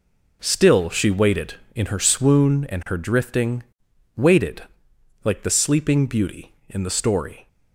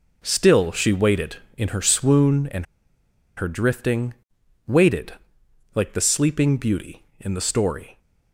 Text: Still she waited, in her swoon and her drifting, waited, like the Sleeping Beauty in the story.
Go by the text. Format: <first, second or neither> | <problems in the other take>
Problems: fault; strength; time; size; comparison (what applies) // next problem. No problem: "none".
first | pauses between "and" and "her"; noticeable; at 2.6 s; 0.72 s long